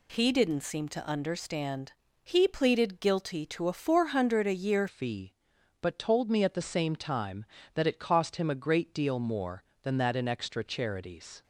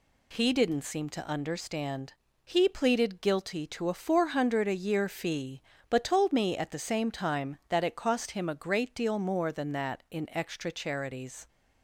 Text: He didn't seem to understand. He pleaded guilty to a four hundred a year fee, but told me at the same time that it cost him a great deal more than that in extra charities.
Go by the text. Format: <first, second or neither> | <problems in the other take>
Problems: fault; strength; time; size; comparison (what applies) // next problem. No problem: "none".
second | changes voice at "fee"; from 4.8 s on; 6.6 s long